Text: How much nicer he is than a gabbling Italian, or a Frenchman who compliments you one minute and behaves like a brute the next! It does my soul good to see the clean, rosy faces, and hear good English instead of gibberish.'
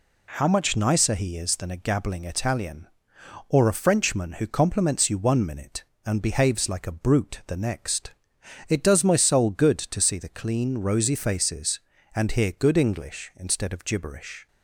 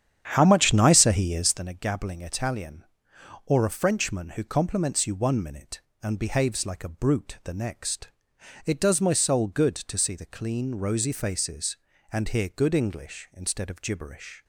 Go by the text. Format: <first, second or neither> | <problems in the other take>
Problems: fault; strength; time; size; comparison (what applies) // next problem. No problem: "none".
first | starts louder than the rest; strong; until 1.7 s; 9 dB